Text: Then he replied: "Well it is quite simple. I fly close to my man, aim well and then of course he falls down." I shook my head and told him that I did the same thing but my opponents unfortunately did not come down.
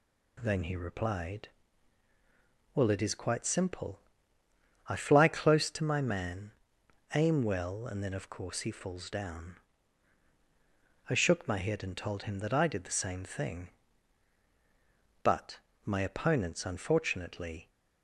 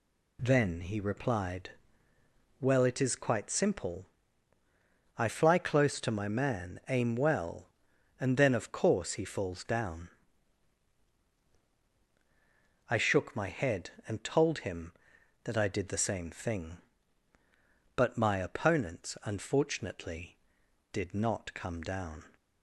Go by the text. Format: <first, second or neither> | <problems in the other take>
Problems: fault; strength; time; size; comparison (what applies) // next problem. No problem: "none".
second | pauses between "but" and "my"; slight; at 15.5 s; 0.26 s long // stops before "did not come down"; at 17.6 s